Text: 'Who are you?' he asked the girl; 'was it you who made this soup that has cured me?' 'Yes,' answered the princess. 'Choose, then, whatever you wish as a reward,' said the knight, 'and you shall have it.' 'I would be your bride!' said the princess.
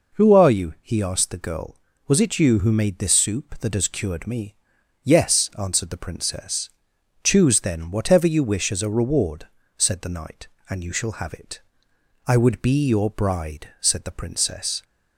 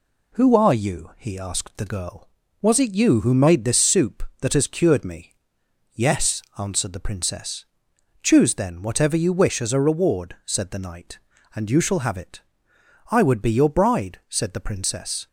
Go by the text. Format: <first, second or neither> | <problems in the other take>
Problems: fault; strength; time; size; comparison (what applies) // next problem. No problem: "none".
neither | none